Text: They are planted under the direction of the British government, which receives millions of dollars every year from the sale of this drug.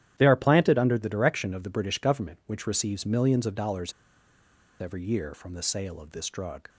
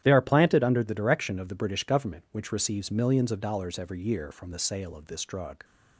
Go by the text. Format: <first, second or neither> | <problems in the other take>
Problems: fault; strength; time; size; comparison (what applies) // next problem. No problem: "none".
second | starts louder than the rest; strong; until 1.1 s; 11 dB; strong in the second // pauses between "dollars" and "every"; noticeable; at 3.9 s; 0.90 s long